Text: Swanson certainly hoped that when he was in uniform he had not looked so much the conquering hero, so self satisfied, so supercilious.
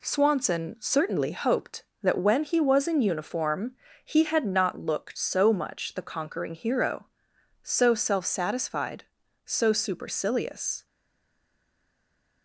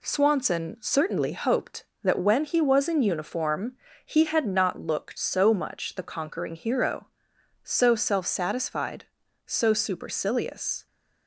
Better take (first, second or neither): second